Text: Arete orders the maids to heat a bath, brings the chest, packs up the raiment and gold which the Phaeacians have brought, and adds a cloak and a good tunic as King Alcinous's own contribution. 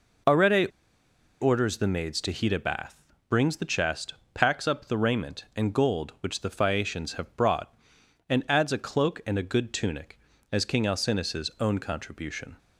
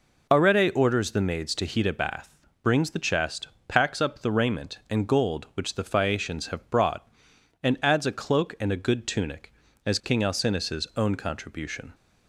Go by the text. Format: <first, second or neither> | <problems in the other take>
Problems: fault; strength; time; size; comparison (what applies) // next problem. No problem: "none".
second | pauses between "Arete" and "orders"; noticeable; at 0.6 s; 0.72 s long